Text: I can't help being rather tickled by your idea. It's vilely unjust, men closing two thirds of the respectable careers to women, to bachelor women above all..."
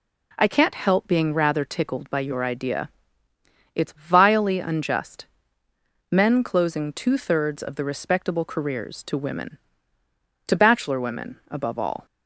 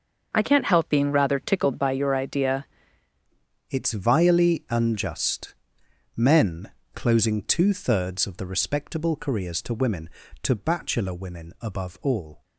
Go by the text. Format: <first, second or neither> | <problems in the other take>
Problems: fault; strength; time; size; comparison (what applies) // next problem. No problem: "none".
first | starts louder than the rest; noticeable; until 1.3 s; 6 dB // changes voice at "It's"; from 3.6 s on; 8.8 s long // pauses between "men" and "closing"; slight; at 6.7 s; 0.24 s long